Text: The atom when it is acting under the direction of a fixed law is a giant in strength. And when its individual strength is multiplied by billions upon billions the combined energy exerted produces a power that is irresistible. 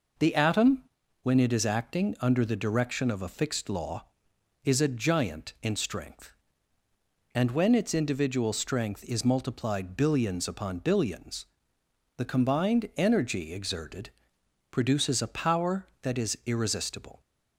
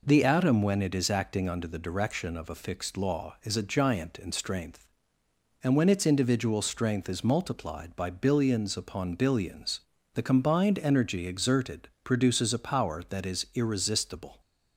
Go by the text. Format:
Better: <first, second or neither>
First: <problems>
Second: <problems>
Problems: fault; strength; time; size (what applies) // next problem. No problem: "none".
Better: second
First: pauses between "atom" and "when"; at 0.8 s; 0.40 s long // skips "by"; at 9.9 s // pauses between "billions" and "the"; noticeable; at 11.4 s; 0.72 s long // pauses between "exerted" and "produces"; noticeable; at 14.0 s; 0.62 s long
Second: pauses between "billions" and "the"; slight; at 9.7 s; 0.32 s long // pauses between "exerted" and "produces"; slight; at 11.8 s; 0.16 s long